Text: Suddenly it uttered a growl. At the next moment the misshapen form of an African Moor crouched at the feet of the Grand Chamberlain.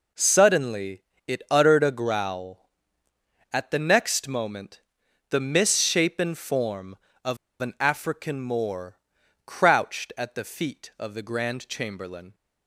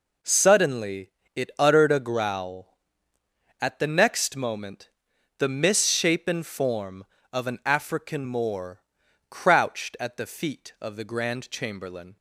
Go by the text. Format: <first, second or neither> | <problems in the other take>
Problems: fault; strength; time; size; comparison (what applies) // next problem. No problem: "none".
second | pauses between "Suddenly" and "it"; slight; at 1.0 s; 0.22 s long; slight in the second // pauses between "moment" and "the"; noticeable; at 4.8 s; 0.48 s long; noticeable in the second // pauses between "of" and "an"; slight; at 7.3 s; 0.25 s long // pauses between "Moor" and "crouched"; noticeable; at 8.9 s; 0.48 s long; noticeable in the second